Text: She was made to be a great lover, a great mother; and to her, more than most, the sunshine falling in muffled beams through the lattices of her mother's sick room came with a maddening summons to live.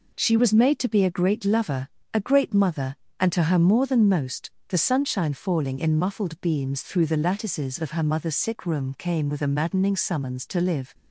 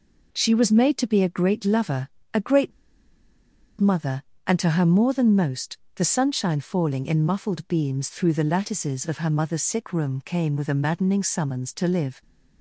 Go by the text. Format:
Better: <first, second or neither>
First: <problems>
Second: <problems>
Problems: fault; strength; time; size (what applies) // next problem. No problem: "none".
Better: first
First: none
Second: pauses between "great" and "mother"; at 2.7 s; 1.0 s long